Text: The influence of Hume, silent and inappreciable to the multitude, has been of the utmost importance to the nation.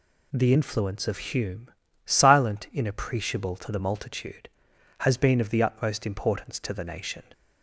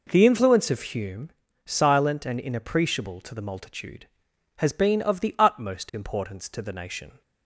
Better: second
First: skips "and"; at 2.6 s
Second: none

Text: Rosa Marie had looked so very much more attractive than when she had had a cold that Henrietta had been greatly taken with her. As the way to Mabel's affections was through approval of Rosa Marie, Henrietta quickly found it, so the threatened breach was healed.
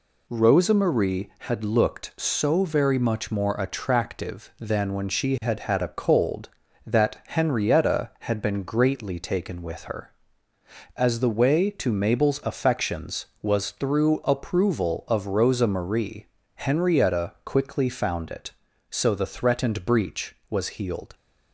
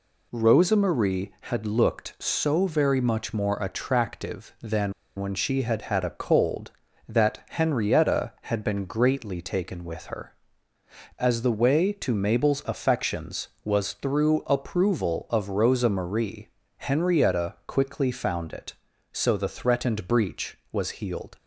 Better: first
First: none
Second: pauses between "than" and "when"; slight; at 4.9 s; 0.26 s long

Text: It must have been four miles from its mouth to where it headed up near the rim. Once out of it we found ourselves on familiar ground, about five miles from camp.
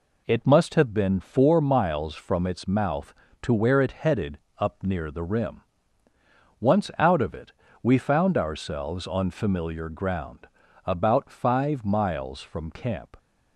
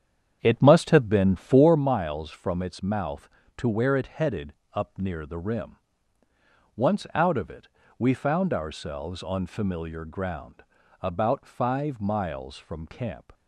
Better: first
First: pauses between "headed" and "up"; slight; at 4.3 s; 0.20 s long // pauses between "it" and "we"; slight; at 7.5 s; 0.30 s long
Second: starts louder than the rest; strong; until 1.9 s; 8.5 dB // pauses between "headed" and "up"; slight; at 4.5 s; 0.20 s long // pauses between "it" and "we"; slight; at 7.6 s; 0.30 s long

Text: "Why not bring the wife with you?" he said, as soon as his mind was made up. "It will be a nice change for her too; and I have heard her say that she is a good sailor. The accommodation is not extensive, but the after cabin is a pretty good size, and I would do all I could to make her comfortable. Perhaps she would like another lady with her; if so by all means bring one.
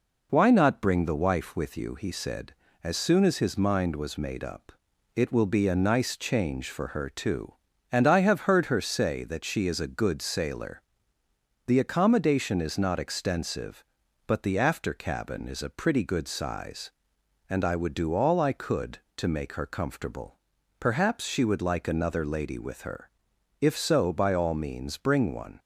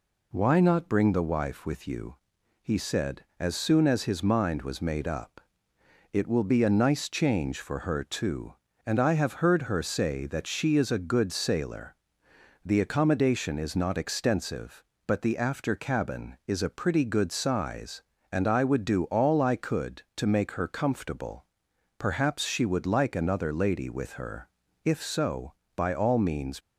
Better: first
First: none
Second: stops before "bring one"; at 26.5 s

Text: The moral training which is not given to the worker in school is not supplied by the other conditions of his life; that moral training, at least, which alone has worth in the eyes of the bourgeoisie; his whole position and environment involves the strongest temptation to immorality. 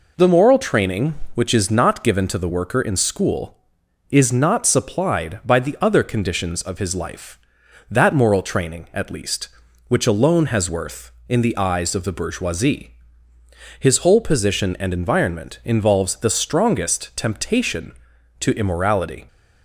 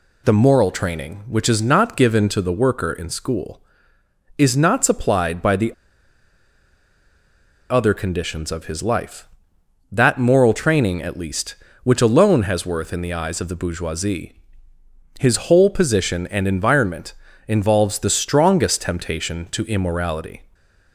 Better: first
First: none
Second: pauses between "the" and "other"; strong; at 5.7 s; 1.9 s long // pauses between "environment" and "involves"; slight; at 17.1 s; 0.34 s long

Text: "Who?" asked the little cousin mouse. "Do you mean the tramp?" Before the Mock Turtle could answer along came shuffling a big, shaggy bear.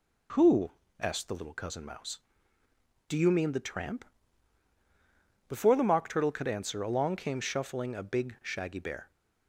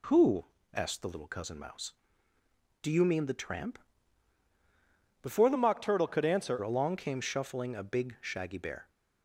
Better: first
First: none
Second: changes voice from "Mock" to "answer"; from 5.5 to 6.5 s; 1.0 s long

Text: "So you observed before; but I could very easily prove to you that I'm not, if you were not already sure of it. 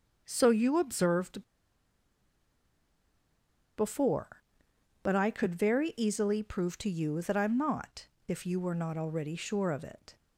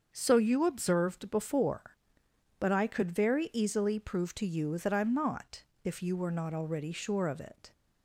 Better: second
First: starts louder than the rest; until 1.2 s; 6.5 dB // pauses between "observed" and "before"; strong; at 1.4 s; 2.3 s long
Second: starts louder than the rest; until 1.1 s; 6.5 dB

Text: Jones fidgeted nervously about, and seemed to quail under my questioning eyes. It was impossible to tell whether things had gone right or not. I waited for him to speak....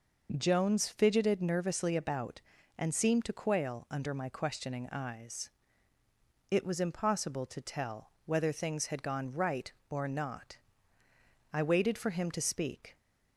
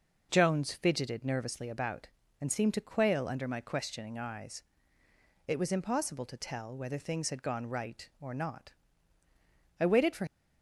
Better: first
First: none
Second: stops before "him to speak"; at 10.2 s

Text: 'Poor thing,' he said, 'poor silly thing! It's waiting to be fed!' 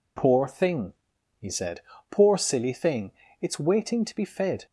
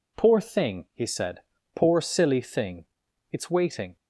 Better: first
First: none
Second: stops before "to be fed"; at 3.9 s

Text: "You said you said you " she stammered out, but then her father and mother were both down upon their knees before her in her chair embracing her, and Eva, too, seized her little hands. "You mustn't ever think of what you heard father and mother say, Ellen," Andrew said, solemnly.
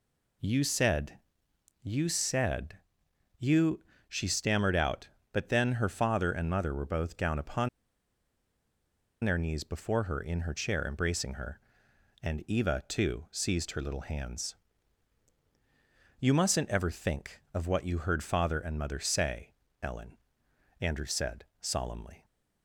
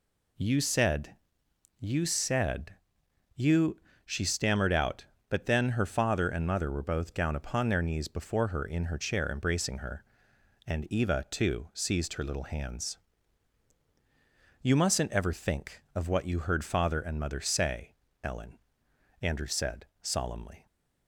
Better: second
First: pauses between "said" and "you"; noticeable; at 1.1 s; 0.64 s long // pauses between "said" and "you"; noticeable; at 2.7 s; 0.60 s long // pauses between "upon" and "their"; strong; at 7.6 s; 1.5 s long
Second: pauses between "said" and "you"; noticeable; at 1.1 s; 0.64 s long // pauses between "said" and "you"; noticeable; at 2.7 s; 0.60 s long

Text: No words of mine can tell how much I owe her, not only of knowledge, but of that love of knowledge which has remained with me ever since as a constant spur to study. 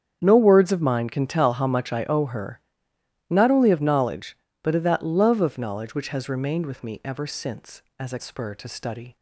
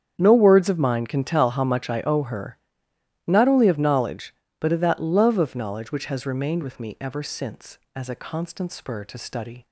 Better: second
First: starts louder than the rest; strong; until 1.2 s; 8 dB // skips "constant"; at 8.2 s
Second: starts louder than the rest; strong; until 1.1 s; 8.5 dB

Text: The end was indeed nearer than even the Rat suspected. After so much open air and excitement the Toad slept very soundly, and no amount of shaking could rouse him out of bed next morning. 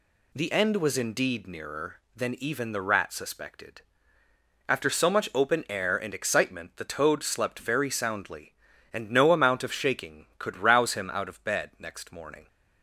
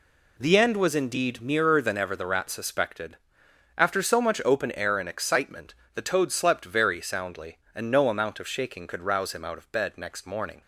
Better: first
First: none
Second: says "ever" for "even"; at 1.9 s // pauses between "excitement" and "the"; slight; at 5.7 s; 0.22 s long

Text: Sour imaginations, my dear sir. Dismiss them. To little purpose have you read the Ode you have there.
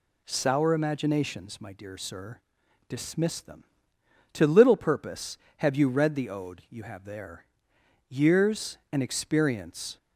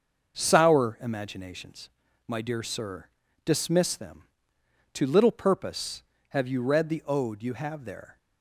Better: second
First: goes on to say "Years and experience"; strong; from 8.0 s on; 1.8 s long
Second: none

